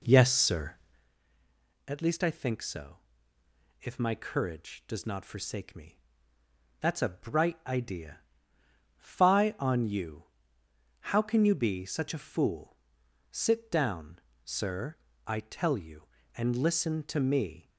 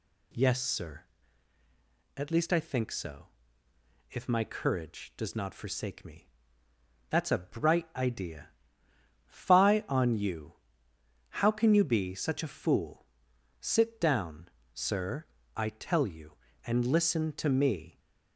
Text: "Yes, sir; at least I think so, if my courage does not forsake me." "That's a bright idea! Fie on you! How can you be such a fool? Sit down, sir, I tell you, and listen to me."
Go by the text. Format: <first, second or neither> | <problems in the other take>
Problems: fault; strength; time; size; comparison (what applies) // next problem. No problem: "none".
second | starts louder than the rest; until 1.1 s; 3.5 dB